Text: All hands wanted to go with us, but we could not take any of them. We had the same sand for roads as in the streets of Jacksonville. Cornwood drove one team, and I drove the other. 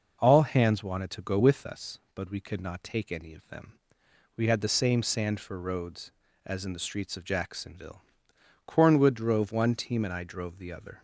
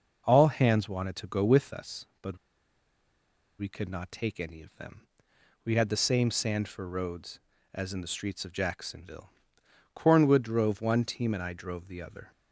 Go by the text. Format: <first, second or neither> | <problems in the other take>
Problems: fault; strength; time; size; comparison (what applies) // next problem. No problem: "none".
first | pauses between "but" and "we"; at 2.3 s; 1.2 s long